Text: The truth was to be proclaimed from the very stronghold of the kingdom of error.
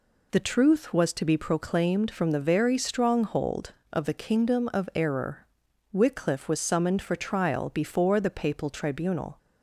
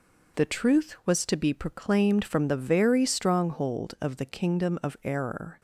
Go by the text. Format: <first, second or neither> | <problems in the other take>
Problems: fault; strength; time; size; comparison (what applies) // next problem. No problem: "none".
second | goes on to say "Wycliffe was summoned for trial before the papal tribunal"; strong; from 5.9 s on; 3.4 s long